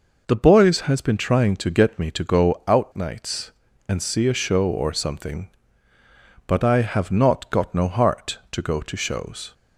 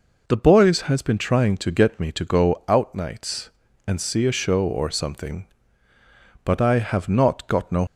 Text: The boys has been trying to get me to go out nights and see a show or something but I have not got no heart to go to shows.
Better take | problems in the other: first | stops before "heart to go to shows"; at 7.8 s

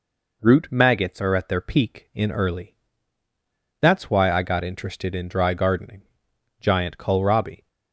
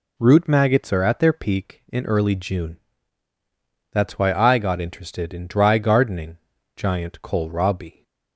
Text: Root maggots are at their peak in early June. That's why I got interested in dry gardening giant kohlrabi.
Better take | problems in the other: second | skips "June"; at 3.2 s // pauses between "gardening" and "giant"; noticeable; at 6.0 s; 0.56 s long; also in the second

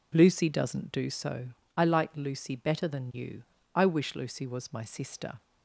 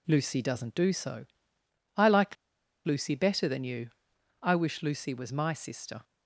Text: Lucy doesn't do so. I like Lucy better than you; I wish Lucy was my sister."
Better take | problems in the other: first | pauses between "like" and "Lucy"; noticeable; at 2.3 s; 0.49 s long

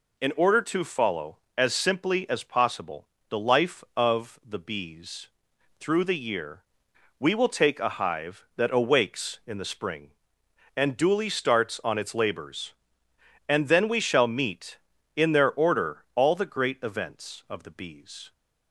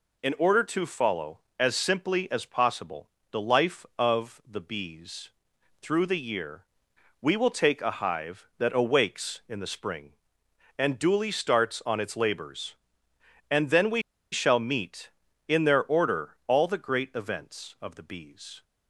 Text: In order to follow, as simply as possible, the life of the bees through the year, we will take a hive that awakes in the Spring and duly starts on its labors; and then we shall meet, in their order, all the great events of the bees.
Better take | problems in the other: first | pauses between "bees" and "through"; noticeable; at 5.2 s; 0.52 s long; noticeable in the first // pauses between "we" and "shall"; slight; at 14.0 s; 0.31 s long

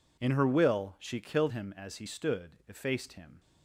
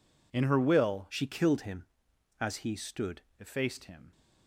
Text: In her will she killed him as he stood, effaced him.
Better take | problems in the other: first | changes voice from "she" to "stood"; from 1.0 to 3.2 s; 2.2 s long

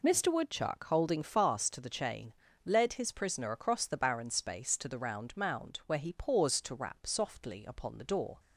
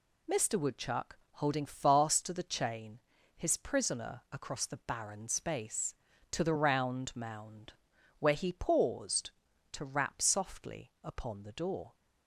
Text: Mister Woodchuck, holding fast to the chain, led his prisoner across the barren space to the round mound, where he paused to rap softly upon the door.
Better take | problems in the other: first | skips "led"; at 3.1 s

